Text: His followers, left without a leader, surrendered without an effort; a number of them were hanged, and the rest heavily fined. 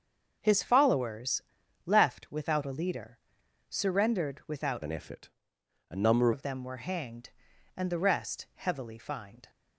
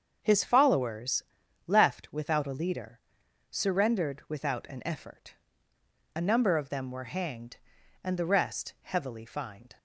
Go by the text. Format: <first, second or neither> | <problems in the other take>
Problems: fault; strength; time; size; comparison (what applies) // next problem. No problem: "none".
second | starts louder than the rest; until 1.4 s; 6.5 dB; also in the second // changes voice from "an" to "number"; from 4.8 to 6.3 s; 1.5 s long